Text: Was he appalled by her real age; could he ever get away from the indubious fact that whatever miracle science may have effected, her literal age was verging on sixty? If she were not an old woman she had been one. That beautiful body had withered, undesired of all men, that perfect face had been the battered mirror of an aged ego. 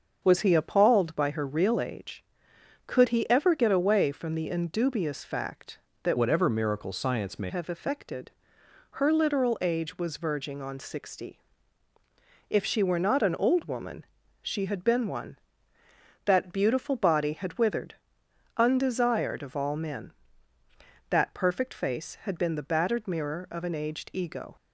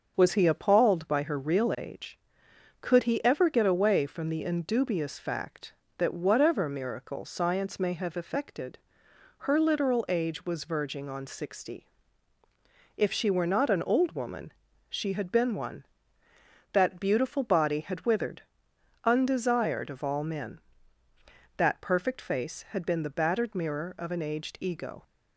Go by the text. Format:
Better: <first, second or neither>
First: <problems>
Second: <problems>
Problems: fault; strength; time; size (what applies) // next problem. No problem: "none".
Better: second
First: starts louder than the rest; until 1.2 s; 6.5 dB // changes voice from "whatever" to "may"; from 6.1 to 7.4 s; 1.3 s long // pauses between "woman" and "she"; slight; at 14.0 s; 0.36 s long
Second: starts louder than the rest; until 1.1 s; 6.5 dB // pauses between "woman" and "she"; slight; at 14.5 s; 0.36 s long